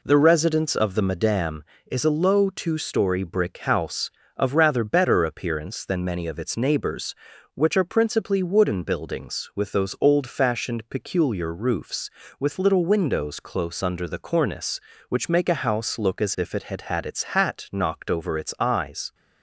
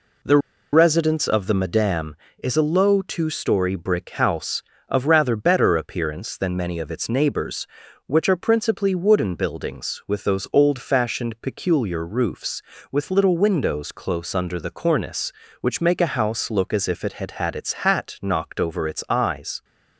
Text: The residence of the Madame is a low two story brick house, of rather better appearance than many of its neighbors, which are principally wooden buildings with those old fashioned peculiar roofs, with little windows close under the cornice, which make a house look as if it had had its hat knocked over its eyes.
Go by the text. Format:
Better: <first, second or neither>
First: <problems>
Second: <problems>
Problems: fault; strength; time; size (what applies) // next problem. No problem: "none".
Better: first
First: none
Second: pauses between "The" and "residence"; slight; at 0.3 s; 0.35 s long